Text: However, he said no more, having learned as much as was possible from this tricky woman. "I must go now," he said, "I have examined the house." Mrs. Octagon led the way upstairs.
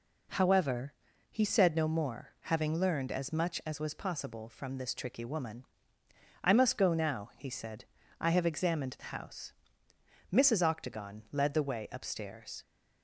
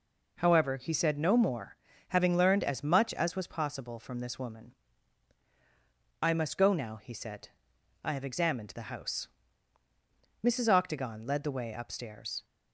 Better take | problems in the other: first | skips "tricky"; at 4.3 s

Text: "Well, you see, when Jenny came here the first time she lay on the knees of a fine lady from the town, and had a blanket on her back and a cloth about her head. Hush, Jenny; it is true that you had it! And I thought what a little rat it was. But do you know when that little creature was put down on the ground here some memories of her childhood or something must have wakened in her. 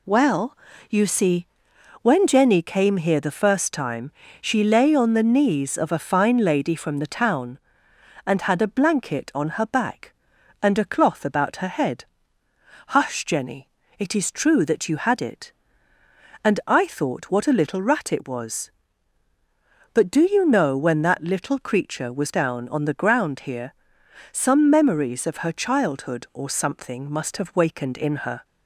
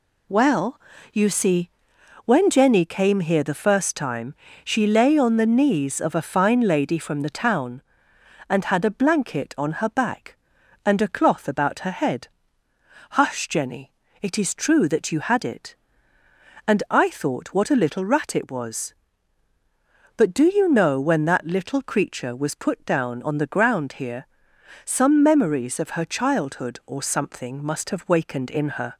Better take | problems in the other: second | pauses between "time" and "she"; slight; at 4.1 s; 0.28 s long; slight in the second // skips "put"; at 22.3 s // pauses between "here" and "some"; noticeable; at 23.7 s; 0.58 s long; noticeable in the second

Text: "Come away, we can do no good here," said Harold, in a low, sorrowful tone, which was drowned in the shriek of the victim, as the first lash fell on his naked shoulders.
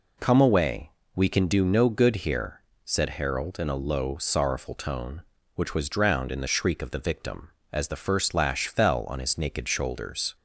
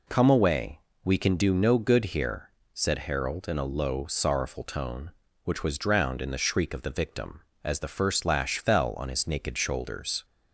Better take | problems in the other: neither | none

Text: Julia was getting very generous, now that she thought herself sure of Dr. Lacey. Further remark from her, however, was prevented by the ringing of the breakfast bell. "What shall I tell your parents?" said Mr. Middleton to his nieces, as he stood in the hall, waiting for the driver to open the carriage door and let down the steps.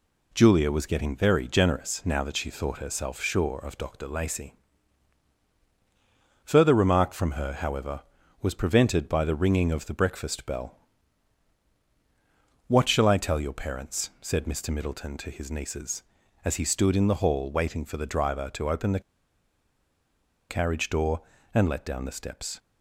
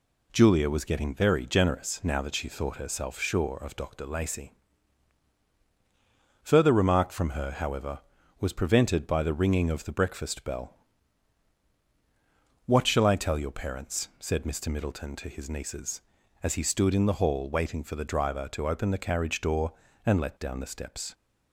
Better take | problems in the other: second | pauses between "the" and "carriage"; strong; at 19.0 s; 1.4 s long

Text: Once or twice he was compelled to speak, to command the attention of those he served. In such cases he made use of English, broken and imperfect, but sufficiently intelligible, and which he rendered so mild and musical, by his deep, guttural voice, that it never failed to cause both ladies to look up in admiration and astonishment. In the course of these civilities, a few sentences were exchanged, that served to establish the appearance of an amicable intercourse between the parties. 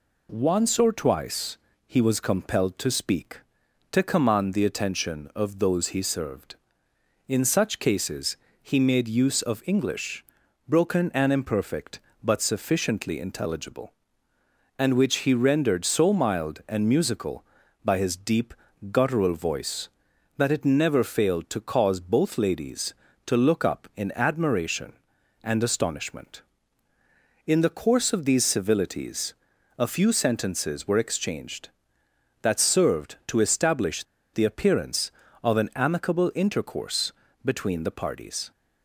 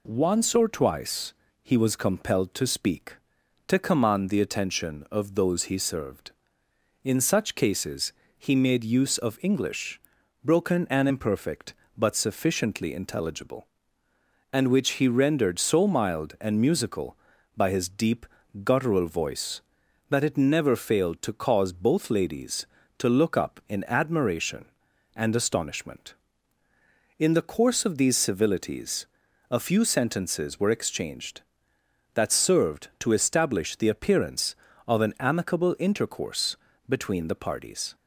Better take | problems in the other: second | pauses between "twice" and "he"; slight; at 1.5 s; 0.30 s long; slight in the second // pauses between "cases" and "he"; slight; at 8.3 s; 0.26 s long; slight in the second // pauses between "establish" and "the"; slight; at 34.0 s; 0.29 s long // pauses between "intercourse" and "between"; slight; at 37.1 s; 0.32 s long; slight in the second

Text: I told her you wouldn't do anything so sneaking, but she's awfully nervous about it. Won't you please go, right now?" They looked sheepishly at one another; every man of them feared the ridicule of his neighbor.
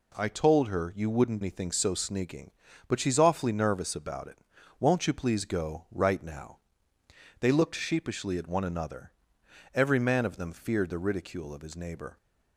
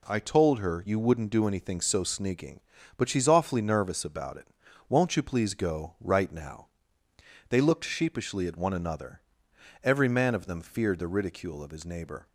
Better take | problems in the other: second | skips "do"; at 1.4 s

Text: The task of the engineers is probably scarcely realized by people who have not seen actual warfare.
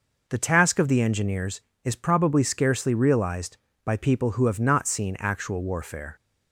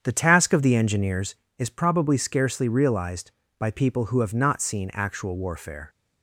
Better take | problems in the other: first | starts louder than the rest; strong; until 1.6 s; 8 dB

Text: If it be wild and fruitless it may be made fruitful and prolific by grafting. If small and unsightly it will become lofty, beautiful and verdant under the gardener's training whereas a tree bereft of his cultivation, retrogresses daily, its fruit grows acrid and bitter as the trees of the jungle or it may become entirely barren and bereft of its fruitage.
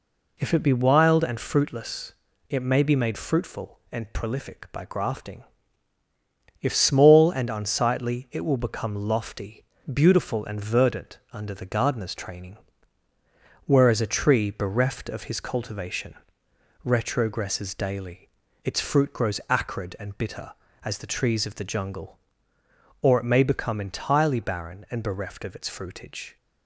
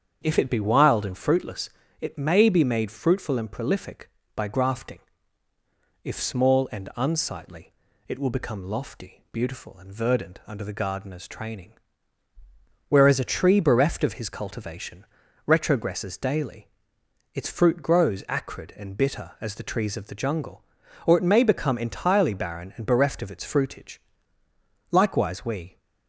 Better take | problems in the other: first | starts louder than the rest; strong; until 1.2 s; 7.5 dB // pauses between "fruitless" and "it"; slight; at 1.6 s; 0.32 s long; slight in the first // pauses between "unsightly" and "it"; slight; at 7.7 s; 0.34 s long // pauses between "training" and "whereas"; at 11.7 s; 1.1 s long; also in the first // goes on to say "Likewise we"; noticeable; from 24.9 s on; 0.86 s long

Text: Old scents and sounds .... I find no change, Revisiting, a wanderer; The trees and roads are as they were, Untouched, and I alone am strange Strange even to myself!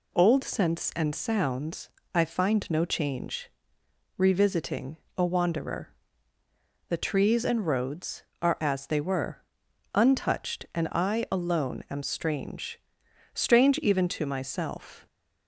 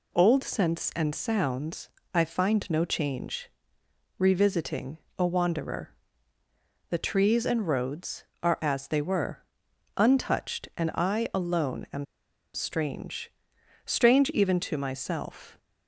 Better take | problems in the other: first | pauses between "am" and "strange"; noticeable; at 12.0 s; 0.49 s long // pauses between "strange" and "Strange"; noticeable; at 13.3 s; 0.54 s long; noticeable in the first

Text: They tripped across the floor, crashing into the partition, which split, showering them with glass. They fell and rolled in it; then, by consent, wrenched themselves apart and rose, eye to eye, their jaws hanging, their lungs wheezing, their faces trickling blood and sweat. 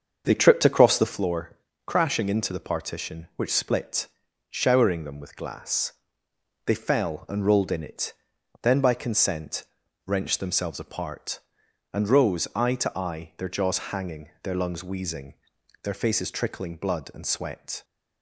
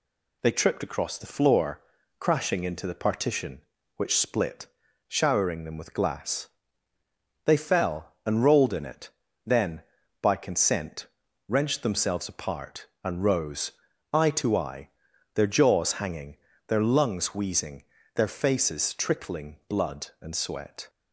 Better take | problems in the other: second | starts louder than the rest; until 1.2 s; 7 dB

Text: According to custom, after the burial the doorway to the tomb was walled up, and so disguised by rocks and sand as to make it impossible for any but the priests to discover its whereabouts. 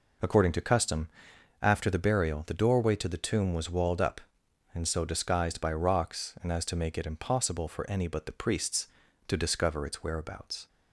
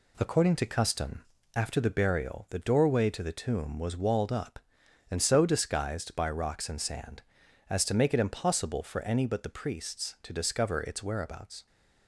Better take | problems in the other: second | skips "sand"; at 6.5 s

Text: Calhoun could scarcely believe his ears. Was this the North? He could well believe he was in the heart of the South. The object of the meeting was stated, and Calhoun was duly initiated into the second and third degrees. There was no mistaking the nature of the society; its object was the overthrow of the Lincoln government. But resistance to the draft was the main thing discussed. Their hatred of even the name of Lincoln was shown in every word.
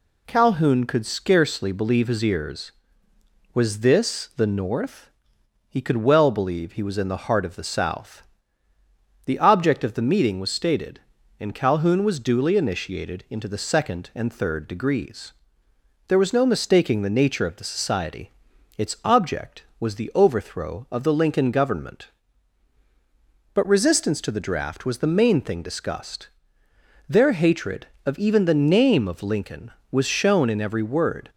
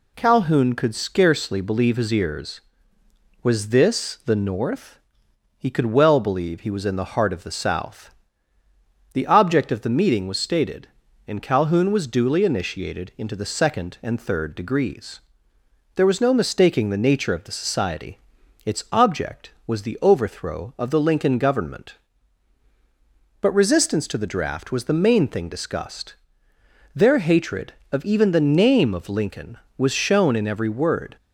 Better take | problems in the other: neither | none

